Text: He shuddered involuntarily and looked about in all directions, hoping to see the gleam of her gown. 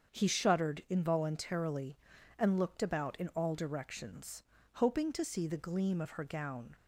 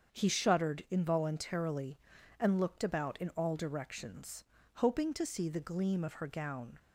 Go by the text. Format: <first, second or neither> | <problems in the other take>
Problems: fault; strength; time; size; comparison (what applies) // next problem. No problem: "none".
neither | starts louder than the rest; strong; the same in both